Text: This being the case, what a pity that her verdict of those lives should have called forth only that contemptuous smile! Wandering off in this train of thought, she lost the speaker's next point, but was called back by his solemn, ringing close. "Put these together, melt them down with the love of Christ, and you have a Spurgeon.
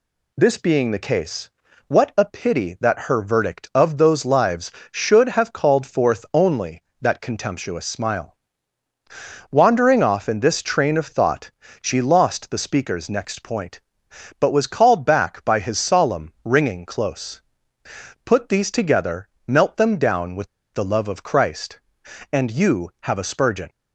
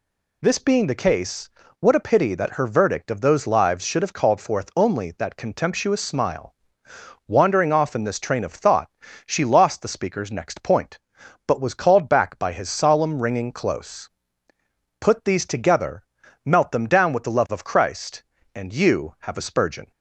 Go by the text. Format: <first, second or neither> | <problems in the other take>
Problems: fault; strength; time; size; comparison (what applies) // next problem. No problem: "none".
second | pauses between "with" and "the"; slight; at 20.4 s; 0.25 s long